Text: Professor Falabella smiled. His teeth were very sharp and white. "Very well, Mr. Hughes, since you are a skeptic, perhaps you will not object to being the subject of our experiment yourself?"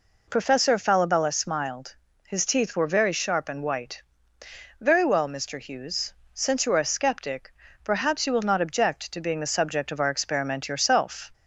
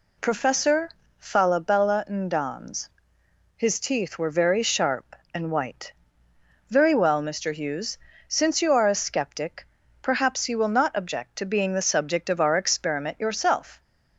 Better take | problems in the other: first | pauses between "Professor" and "Falabella"; slight; at 0.8 s; 0.30 s long // says "ndans" for "smiled"; at 2.0 s

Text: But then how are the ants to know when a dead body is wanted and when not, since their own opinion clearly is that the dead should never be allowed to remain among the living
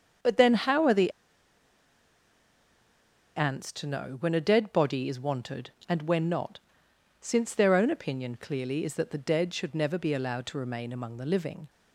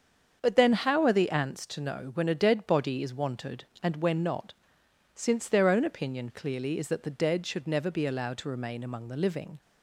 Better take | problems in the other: second | starts louder than the rest; strong; until 3.5 s; 7 dB; also in the second // pauses between "the" and "ants"; strong; at 1.1 s; 2.2 s long

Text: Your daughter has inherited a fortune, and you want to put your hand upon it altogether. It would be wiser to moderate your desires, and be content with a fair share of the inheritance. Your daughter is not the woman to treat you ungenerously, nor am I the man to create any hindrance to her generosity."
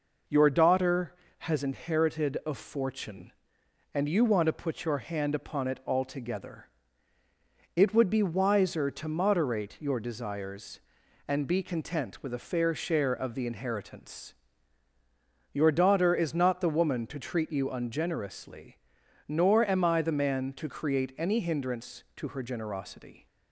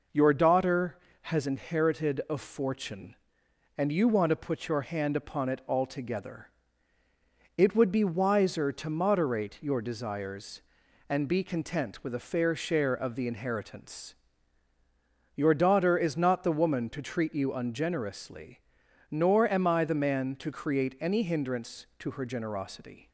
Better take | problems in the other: neither | none

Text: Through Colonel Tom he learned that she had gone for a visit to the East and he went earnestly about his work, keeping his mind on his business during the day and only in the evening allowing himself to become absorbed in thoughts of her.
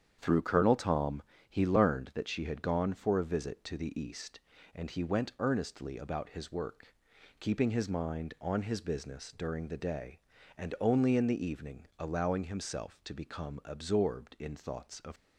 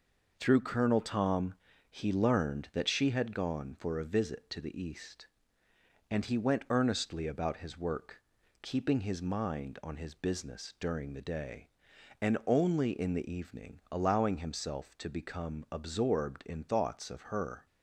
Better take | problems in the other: second | starts louder than the rest; strong; until 1.2 s; 8.5 dB // pauses between "Tom" and "he"; slight; at 1.2 s; 0.26 s long; slight in the second // stops before "her"; at 15.1 s

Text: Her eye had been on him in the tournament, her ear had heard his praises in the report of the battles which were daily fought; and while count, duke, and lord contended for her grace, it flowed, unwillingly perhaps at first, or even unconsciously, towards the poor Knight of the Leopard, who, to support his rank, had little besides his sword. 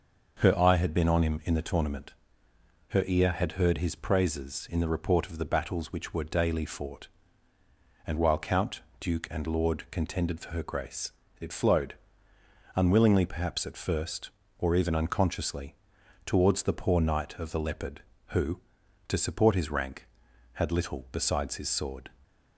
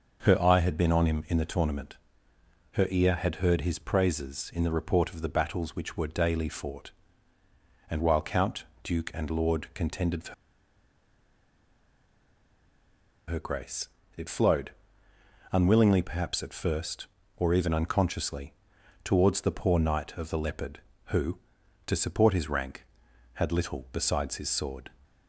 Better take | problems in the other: first | starts louder than the rest; noticeable; until 1.2 s; 6 dB; noticeable in the first // pauses between "for" and "her"; strong; at 10.3 s; 2.9 s long

